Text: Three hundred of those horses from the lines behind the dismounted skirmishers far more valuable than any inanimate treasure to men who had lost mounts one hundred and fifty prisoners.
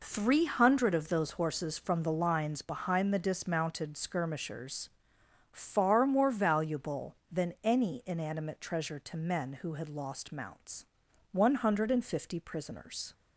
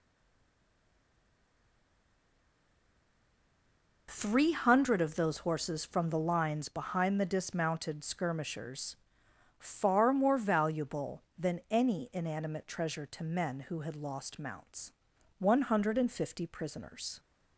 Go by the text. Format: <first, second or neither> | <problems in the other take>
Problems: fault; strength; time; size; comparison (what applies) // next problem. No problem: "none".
first | stays silent before the first word; strong; until 4.0 s; 4.0 s long // pauses between "skirmishers" and "far"; noticeable; at 8.9 s; 0.64 s long; noticeable in the first // pauses between "mounts" and "one"; noticeable; at 14.9 s; 0.46 s long; noticeable in the first